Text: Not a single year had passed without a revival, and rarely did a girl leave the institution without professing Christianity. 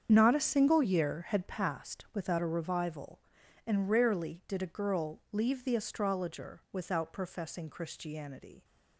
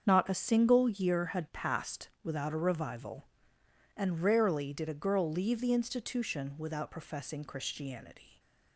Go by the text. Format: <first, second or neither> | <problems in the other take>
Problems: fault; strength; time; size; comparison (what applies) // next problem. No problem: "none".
second | starts louder than the rest; strong; until 1.1 s; 7.5 dB; strong in the second // says "astrologer" for "institution"; at 5.7 s